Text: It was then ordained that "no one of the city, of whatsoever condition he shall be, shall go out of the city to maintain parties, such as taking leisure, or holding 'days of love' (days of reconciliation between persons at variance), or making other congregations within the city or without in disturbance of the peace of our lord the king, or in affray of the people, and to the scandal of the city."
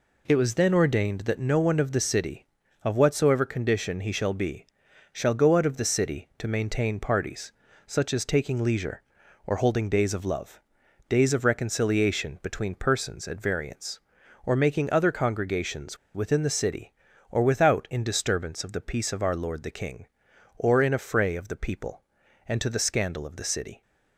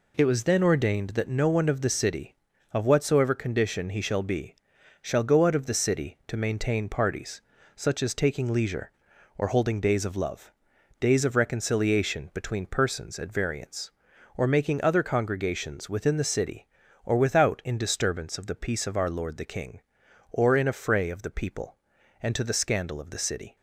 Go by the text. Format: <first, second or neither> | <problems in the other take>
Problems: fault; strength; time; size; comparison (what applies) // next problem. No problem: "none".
second | pauses between "congregations" and "within"; slight; at 15.9 s; 0.18 s long